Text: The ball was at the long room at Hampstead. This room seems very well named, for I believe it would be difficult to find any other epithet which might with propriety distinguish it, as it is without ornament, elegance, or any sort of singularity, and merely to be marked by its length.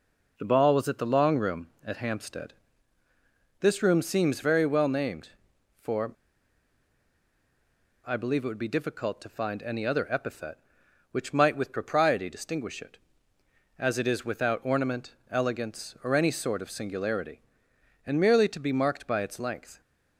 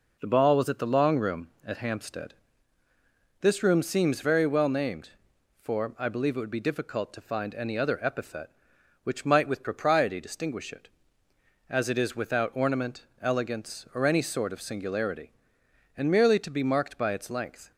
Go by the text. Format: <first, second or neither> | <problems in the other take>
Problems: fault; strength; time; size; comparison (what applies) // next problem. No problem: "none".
second | pauses between "for" and "I"; strong; at 6.1 s; 1.9 s long